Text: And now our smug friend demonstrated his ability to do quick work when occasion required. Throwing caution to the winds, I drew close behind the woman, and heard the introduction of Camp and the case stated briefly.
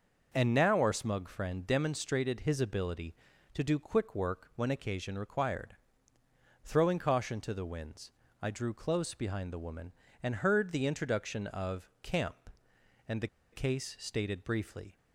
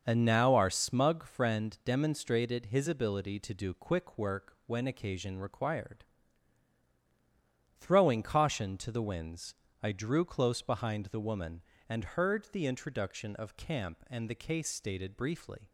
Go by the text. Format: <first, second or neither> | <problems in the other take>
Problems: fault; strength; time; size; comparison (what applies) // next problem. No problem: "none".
second | pauses between "the" and "case"; slight; at 13.2 s; 0.25 s long